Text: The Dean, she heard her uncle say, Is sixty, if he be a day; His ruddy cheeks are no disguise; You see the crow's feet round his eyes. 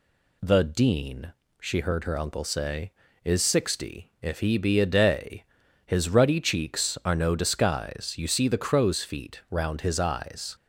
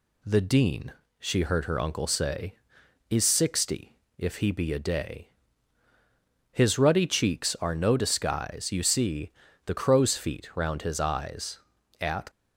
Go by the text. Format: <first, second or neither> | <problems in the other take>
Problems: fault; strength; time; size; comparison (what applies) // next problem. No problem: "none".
first | pauses between "see" and "the"; slight; at 9.3 s; 0.34 s long // goes on to say "At"; slight; from 11.9 s on; 0.30 s long